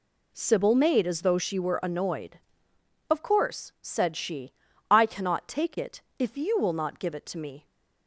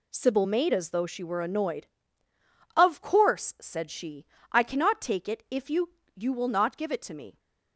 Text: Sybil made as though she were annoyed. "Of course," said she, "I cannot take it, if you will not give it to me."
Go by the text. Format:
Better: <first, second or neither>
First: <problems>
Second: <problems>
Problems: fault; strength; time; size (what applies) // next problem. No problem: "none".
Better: first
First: none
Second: says "you" twice; at 6.1 s